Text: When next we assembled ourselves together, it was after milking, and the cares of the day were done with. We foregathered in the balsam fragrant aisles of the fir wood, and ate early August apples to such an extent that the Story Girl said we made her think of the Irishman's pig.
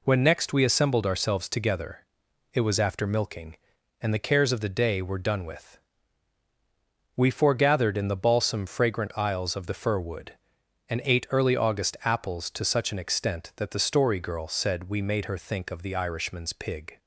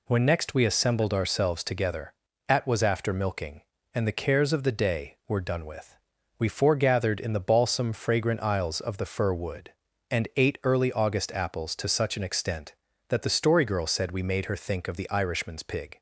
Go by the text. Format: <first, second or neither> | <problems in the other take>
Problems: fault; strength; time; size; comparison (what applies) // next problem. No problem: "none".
first | says "at" for "it"; at 2.4 s